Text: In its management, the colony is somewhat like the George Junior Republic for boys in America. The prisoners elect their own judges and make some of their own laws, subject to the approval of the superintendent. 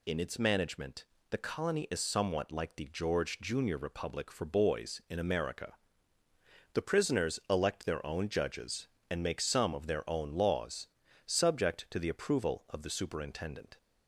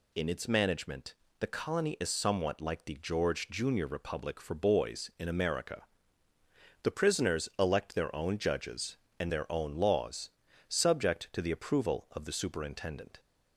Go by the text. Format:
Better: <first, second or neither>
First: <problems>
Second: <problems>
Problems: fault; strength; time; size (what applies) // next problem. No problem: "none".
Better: first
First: none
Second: skips "make some of"; at 9.3 s